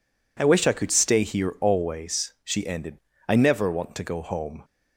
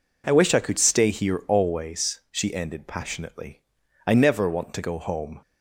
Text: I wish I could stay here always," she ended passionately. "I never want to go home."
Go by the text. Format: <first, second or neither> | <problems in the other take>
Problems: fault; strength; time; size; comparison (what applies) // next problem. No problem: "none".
second | skips "passionately"; at 3.1 s